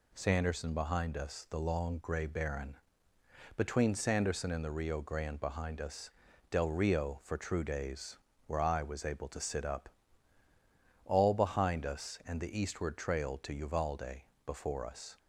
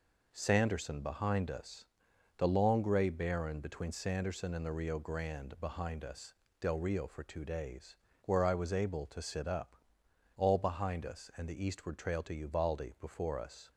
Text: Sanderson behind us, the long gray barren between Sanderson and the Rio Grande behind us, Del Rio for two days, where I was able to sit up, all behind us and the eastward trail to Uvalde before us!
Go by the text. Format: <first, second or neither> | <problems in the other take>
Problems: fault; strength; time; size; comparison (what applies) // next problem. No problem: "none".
second | pauses between "barren" and "between"; noticeable; at 2.7 s; 0.80 s long // says "true" for "two"; at 7.3 s // pauses between "Uvalde" and "before"; slight; at 14.2 s; 0.24 s long